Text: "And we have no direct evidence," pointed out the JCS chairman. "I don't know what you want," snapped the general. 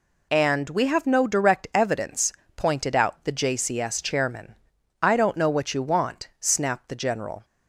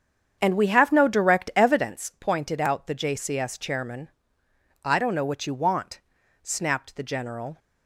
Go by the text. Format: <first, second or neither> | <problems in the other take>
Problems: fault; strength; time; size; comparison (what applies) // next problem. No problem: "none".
first | starts louder than the rest; strong; until 2.0 s; 8 dB